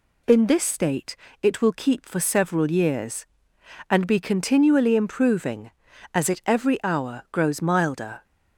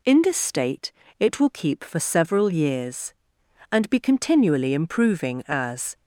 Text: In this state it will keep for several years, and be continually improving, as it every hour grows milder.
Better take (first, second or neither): first